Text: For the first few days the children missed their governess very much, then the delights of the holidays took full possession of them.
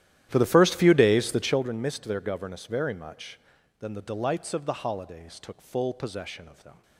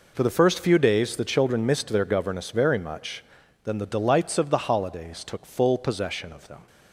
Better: second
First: starts louder than the rest; strong; until 1.7 s; 12.5 dB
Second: none

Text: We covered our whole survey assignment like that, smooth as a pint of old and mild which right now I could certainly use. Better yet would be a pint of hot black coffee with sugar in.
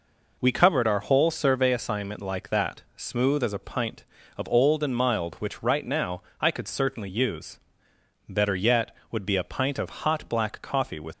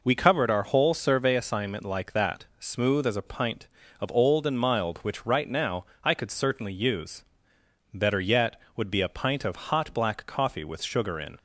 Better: second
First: pauses between "now" and "I"; slight; at 6.2 s; 0.18 s long // stops before "sugar in"; at 11.1 s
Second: pauses between "now" and "I"; slight; at 5.8 s; 0.18 s long

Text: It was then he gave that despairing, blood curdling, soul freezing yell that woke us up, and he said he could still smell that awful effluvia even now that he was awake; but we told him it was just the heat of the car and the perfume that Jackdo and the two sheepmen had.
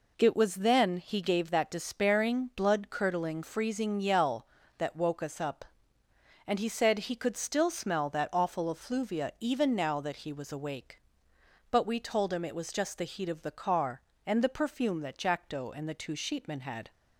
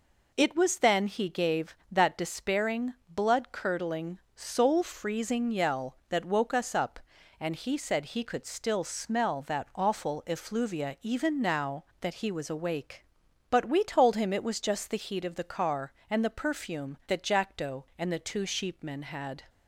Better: second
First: skips "soul"; at 3.4 s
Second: none

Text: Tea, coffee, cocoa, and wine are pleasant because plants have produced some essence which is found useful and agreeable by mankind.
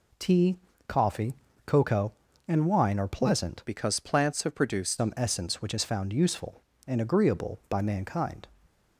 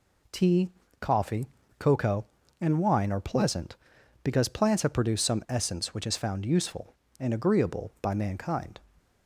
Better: second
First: changes voice from "because" to "produced"; from 3.6 to 4.9 s; 1.3 s long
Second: none

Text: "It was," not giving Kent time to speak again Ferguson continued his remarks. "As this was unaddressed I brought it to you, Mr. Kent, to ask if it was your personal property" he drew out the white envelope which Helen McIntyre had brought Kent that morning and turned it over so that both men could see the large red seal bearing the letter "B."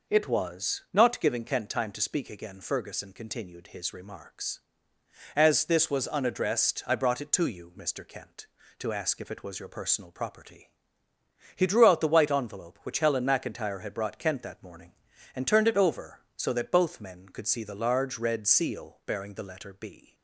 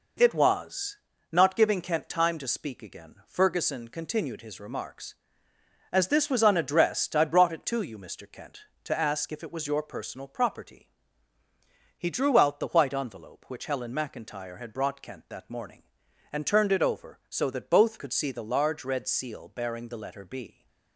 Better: first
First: pauses between "property" and "he"; noticeable; at 10.7 s; 0.86 s long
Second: pauses between "property" and "he"; at 10.8 s; 1.0 s long // skips "men"; at 17.9 s

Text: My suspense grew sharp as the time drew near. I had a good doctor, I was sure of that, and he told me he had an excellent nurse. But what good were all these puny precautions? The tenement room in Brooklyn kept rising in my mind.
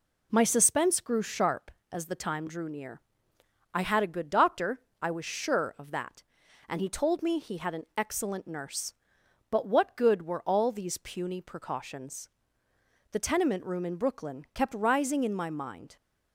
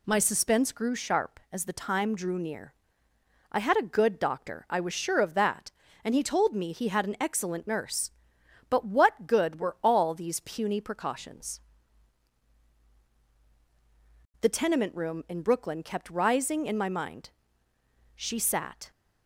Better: first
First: none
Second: goes on to say "She sat"; noticeable; from 18.1 s on; 0.76 s long

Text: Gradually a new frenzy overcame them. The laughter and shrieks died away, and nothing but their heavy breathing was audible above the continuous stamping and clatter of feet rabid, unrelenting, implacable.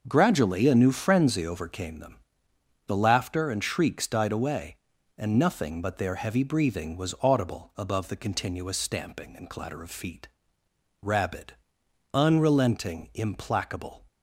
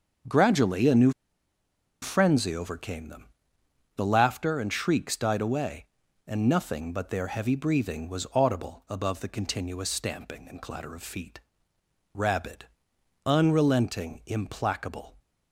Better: first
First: starts louder than the rest; noticeable; until 1.0 s; 6 dB // pauses between "feet" and "rabid"; noticeable; at 10.2 s; 0.74 s long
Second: starts louder than the rest; until 2.2 s; 6.5 dB // pauses between "new" and "frenzy"; noticeable; at 1.1 s; 0.91 s long // pauses between "feet" and "rabid"; noticeable; at 11.3 s; 0.74 s long

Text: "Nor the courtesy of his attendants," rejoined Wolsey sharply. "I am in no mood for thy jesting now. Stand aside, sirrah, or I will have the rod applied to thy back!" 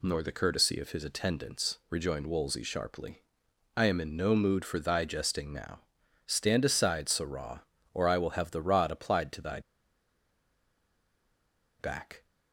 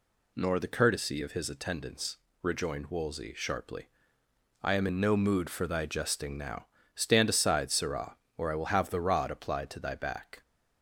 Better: second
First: pauses between "thy" and "back"; strong; at 9.5 s; 2.2 s long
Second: none

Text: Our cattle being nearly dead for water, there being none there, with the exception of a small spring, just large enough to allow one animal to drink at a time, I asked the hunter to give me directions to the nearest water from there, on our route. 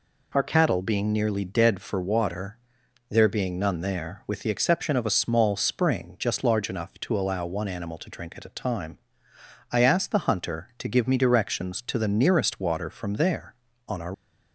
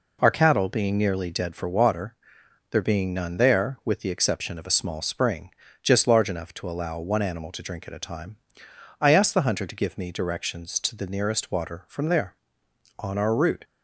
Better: second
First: stops before "route"; at 14.1 s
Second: none

